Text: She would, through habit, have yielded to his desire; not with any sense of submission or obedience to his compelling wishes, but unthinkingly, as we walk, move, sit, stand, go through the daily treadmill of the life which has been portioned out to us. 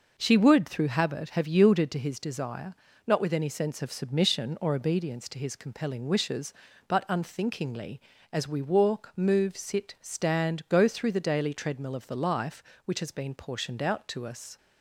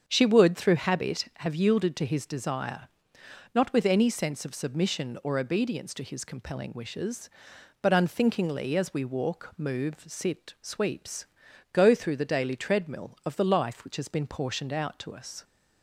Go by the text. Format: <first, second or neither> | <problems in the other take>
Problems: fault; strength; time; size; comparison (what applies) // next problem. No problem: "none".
first | starts louder than the rest; strong; until 1.0 s; 7 dB // says "sweeps" for "stand"; at 10.6 s